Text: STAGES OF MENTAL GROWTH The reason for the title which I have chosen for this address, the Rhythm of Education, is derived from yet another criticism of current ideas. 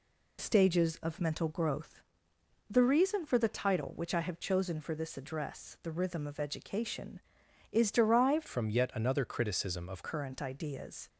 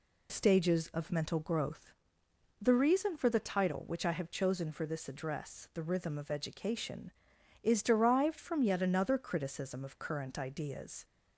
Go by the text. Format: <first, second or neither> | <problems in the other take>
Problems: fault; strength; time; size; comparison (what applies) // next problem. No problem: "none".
second | pauses between "GROWTH" and "The"; noticeable; at 2.0 s; 0.68 s long; noticeable in the second // changes voice from "from" to "of"; from 8.4 to 10.0 s; 1.6 s long